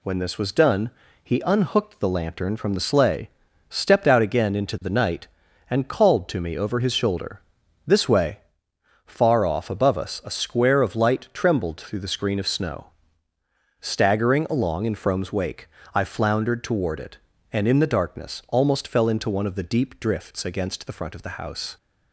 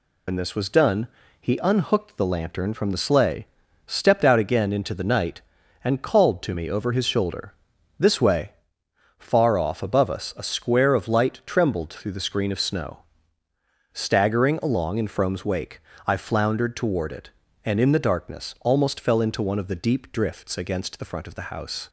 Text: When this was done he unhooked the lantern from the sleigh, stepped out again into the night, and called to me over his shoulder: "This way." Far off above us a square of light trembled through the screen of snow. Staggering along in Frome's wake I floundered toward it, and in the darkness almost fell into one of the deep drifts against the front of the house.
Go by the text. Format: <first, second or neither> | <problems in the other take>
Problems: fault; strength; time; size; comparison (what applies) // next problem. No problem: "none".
first | loses the start of "When"; at 0.2 s; 75 ms // pauses between "done" and "he"; slight; at 1.0 s; 0.34 s long; slight in the first // pauses between "wake" and "I"; slight; at 15.8 s; 0.26 s long; slight in the first